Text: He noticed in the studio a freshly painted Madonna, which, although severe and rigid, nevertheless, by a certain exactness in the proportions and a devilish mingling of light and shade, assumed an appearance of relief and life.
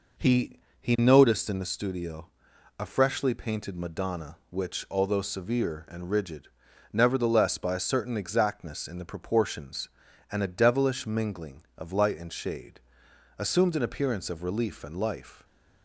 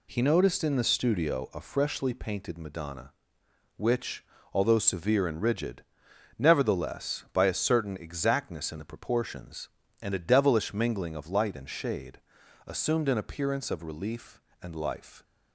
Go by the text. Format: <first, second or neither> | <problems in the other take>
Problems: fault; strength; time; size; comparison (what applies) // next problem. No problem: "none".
second | says "He" twice; at 0.7 s // pauses between "studio" and "a"; noticeable; at 2.2 s; 0.50 s long